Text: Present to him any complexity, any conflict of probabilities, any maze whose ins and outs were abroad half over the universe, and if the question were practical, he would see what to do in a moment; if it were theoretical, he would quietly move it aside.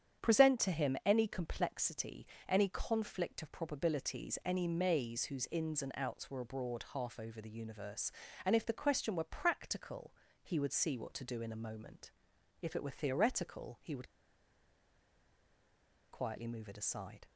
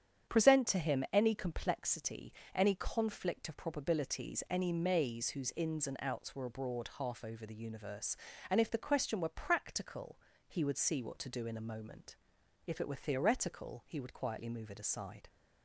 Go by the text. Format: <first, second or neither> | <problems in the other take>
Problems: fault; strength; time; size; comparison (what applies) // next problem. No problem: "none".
second | starts louder than the rest; strong; until 1.3 s; 8.5 dB; strong in the second // pauses between "would" and "quietly"; strong; at 14.0 s; 2.0 s long